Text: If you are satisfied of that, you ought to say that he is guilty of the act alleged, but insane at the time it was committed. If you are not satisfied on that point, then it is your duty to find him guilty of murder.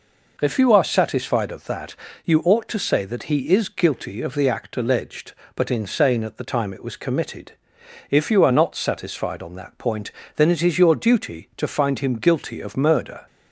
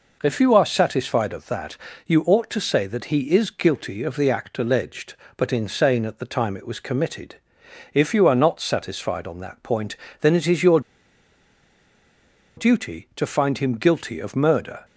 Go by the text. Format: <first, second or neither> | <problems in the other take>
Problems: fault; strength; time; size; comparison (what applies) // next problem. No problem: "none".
first | pauses between "your" and "duty"; strong; at 10.8 s; 1.7 s long